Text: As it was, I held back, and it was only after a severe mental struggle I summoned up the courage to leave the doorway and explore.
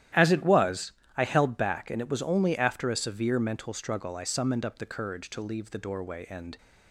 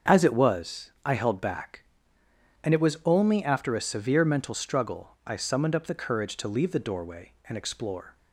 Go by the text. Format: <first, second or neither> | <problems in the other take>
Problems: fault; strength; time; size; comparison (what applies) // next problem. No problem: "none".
second | starts louder than the rest; strong; until 1.4 s; 12.5 dB; also in the second // stops before "explore"; at 6.5 s